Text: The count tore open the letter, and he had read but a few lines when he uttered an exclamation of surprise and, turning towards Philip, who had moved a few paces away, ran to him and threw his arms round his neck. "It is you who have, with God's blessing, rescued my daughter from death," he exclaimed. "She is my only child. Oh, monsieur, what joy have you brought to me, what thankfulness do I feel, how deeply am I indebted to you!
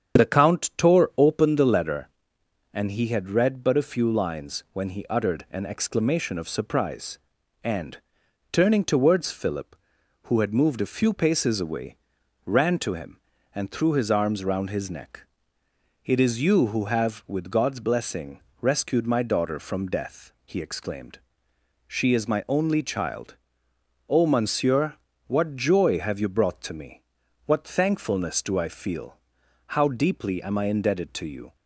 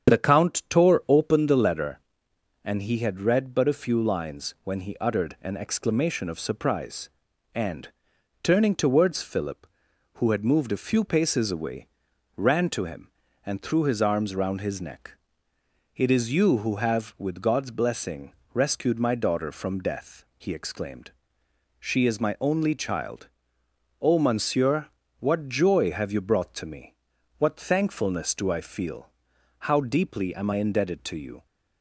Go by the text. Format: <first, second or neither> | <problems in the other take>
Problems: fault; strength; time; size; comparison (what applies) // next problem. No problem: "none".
neither | starts louder than the rest; strong; the same in both